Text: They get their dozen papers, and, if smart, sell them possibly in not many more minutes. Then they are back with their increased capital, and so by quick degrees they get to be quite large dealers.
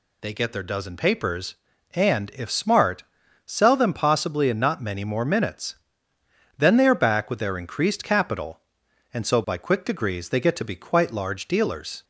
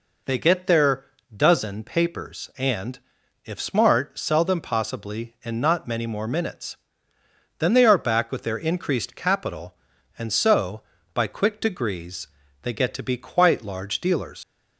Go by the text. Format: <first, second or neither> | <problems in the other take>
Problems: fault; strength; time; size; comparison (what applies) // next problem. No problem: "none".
first | pauses between "their" and "dozen"; slight; at 1.0 s; 0.28 s long // pauses between "degrees" and "they"; slight; at 12.2 s; 0.34 s long // leaves "dealers" unfinished; at 14.4 s; 100 ms